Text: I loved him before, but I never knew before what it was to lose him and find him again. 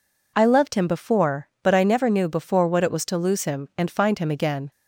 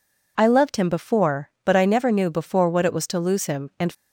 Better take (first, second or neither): first